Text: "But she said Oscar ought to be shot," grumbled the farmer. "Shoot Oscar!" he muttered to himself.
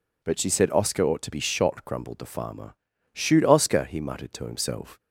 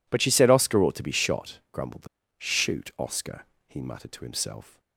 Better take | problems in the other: first | skips "farmer"; at 2.2 s

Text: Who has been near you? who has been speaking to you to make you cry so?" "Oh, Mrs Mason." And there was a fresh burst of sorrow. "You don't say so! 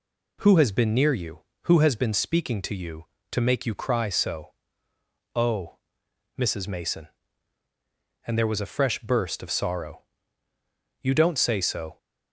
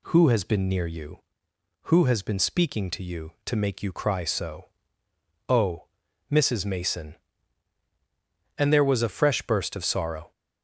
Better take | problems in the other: first | stops before "You don't say so"; at 10.3 s

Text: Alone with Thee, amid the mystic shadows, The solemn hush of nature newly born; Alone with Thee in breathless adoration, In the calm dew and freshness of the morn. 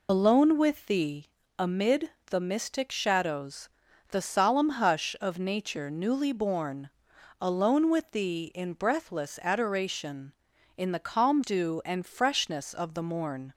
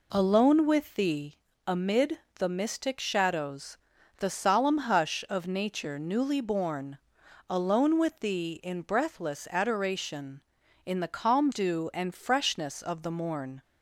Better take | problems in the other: second | loses the start of "Alone"; at 0.0 s; 75 ms // pauses between "amid" and "the"; slight; at 2.1 s; 0.18 s long; slight in the second

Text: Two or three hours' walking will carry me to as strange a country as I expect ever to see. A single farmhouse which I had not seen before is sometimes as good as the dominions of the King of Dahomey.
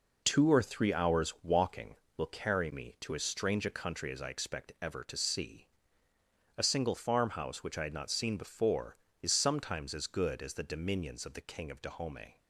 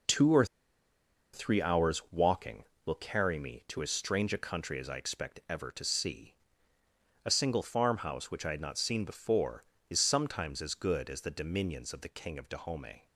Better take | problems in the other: first | pauses between "or" and "three"; noticeable; at 0.4 s; 0.88 s long

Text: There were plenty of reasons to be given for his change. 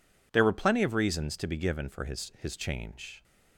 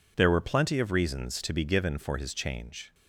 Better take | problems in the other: second | says "his" twice; at 2.3 s

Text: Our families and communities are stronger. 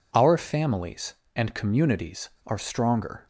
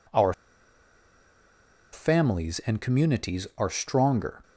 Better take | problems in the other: first | pauses between "Our" and "families"; strong; at 0.3 s; 1.6 s long

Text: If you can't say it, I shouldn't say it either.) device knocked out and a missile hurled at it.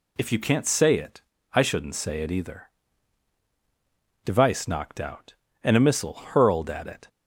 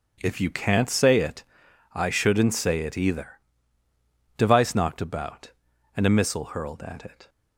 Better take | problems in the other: first | starts louder than the rest; until 1.2 s; 7 dB // says "about" for "out"; at 5.0 s

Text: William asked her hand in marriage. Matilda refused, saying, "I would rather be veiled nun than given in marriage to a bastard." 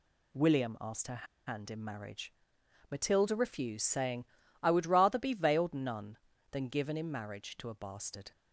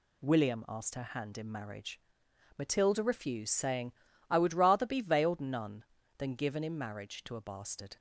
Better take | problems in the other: second | pauses between "her" and "hand"; slight; at 1.2 s; 0.20 s long

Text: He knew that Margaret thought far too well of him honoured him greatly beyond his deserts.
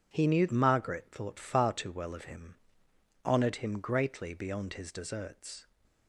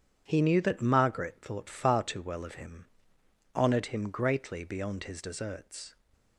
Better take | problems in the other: second | skips "that"; at 0.4 s // pauses between "him" and "honoured"; noticeable; at 2.5 s; 0.68 s long; noticeable in the second

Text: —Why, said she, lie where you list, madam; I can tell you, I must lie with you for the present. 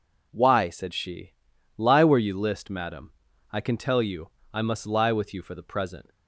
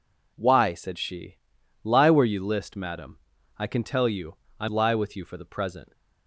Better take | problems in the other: first | skips "must"; at 4.6 s

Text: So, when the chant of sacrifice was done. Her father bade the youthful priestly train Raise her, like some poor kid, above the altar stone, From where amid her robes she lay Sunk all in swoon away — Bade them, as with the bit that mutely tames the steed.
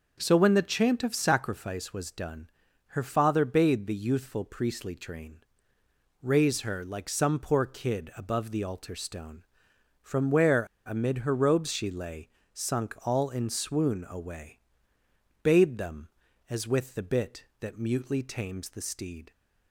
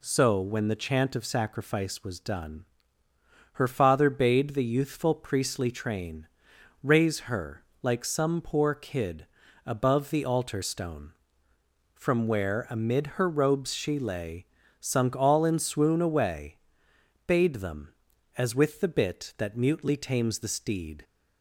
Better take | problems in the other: second | starts louder than the rest; until 1.2 s; 6.5 dB // pauses between "train" and "Raise"; noticeable; at 5.3 s; 0.84 s long; noticeable in the second // pauses between "where" and "amid"; slight; at 10.6 s; 0.21 s long // pauses between "lay" and "Sunk"; slight; at 12.2 s; 0.24 s long; slight in the second

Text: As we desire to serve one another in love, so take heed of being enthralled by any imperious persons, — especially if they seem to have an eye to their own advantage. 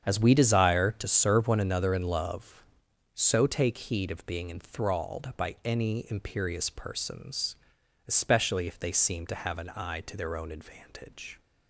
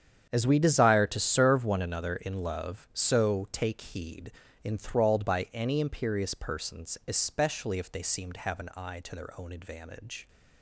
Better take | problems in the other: first | starts louder than the rest; strong; until 1.3 s; 8.5 dB; strong in the first // skips "of being"; at 4.4 s

